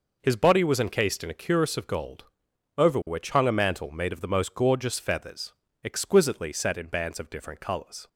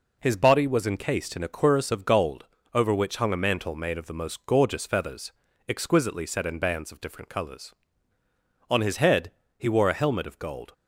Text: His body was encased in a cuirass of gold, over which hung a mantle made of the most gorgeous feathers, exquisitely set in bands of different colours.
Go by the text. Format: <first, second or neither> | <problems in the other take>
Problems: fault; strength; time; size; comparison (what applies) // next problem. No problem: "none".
first | goes on to say "On his head he wore a helmet of gold"; strong; from 8.6 s on; 2.0 s long